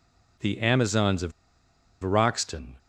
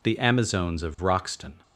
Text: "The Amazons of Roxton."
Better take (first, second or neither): second